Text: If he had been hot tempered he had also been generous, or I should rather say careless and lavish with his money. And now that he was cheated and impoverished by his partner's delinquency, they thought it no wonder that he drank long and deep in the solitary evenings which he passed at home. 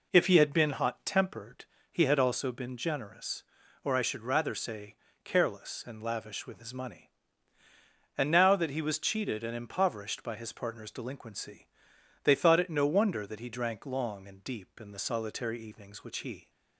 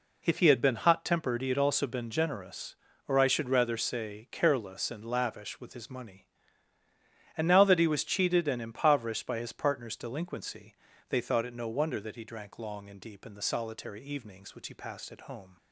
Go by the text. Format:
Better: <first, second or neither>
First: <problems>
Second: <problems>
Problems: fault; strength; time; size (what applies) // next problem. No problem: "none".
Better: second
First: pauses between "tempered" and "he"; slight; at 1.6 s; 0.26 s long // pauses between "say" and "careless"; slight; at 4.9 s; 0.28 s long // stops before "passed at home"; at 16.4 s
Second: none